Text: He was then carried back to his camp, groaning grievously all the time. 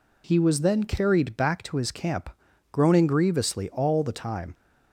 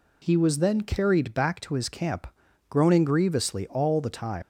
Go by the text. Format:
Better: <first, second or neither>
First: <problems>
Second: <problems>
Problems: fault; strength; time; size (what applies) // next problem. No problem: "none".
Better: first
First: none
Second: leaves "time" unfinished; at 4.4 s; 90 ms